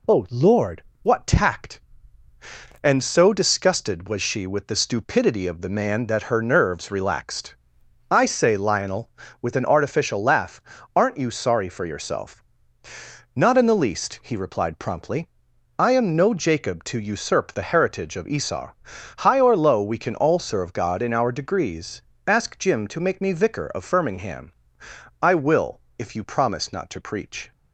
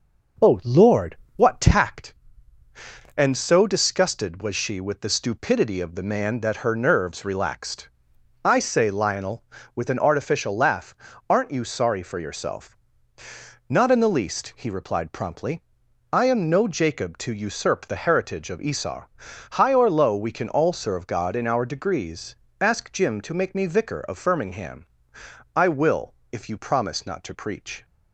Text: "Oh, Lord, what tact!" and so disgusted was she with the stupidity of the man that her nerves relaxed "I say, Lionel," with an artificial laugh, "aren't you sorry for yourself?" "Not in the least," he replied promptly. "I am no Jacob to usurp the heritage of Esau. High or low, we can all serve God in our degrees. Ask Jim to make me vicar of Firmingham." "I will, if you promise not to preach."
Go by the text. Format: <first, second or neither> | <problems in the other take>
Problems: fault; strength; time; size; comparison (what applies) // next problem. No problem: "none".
first | starts louder than the rest; noticeable; until 1.9 s; 6 dB // pauses between "relaxed" and "I"; noticeable; at 7.8 s; 0.54 s long; noticeable in the first